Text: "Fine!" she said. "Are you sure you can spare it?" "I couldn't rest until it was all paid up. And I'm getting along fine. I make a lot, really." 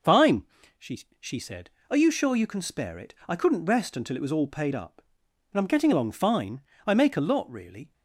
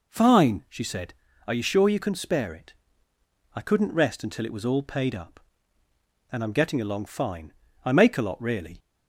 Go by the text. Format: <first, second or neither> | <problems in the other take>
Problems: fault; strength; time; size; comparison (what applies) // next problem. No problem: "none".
second | says "she" twice; at 1.1 s